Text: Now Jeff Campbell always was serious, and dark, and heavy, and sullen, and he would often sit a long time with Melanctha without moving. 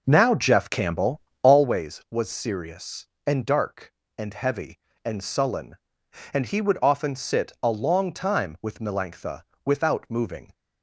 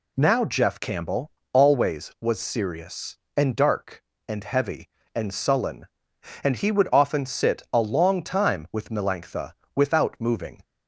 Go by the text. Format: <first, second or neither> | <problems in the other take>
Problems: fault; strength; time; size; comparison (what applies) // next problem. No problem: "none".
second | starts louder than the rest; noticeable; until 1.6 s; 5.5 dB // pauses between "Campbell" and "always"; slight; at 1.2 s; 0.20 s long; slight in the second // pauses between "Melanctha" and "without"; slight; at 9.4 s; 0.20 s long; slight in the second